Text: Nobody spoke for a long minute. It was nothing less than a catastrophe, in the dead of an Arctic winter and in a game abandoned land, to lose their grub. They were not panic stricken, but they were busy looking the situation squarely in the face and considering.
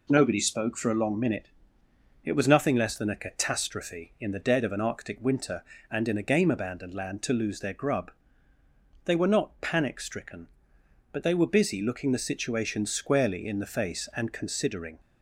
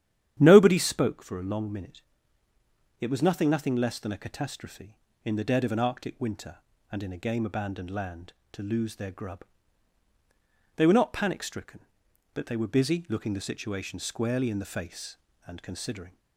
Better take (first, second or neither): first